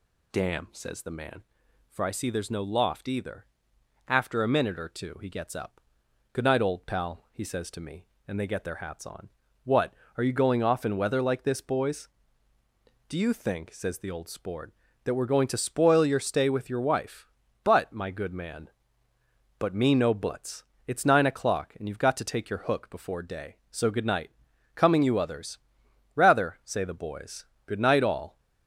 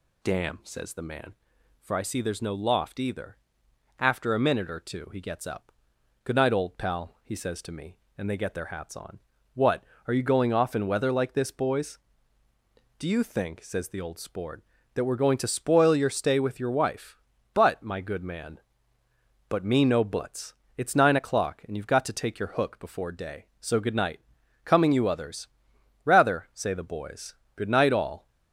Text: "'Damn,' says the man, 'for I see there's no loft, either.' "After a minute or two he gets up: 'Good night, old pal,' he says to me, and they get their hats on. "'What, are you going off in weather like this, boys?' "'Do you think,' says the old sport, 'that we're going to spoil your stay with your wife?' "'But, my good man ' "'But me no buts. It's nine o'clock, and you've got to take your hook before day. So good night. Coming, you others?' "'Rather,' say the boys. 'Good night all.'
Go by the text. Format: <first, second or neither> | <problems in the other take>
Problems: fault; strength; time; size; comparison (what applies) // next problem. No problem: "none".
neither | none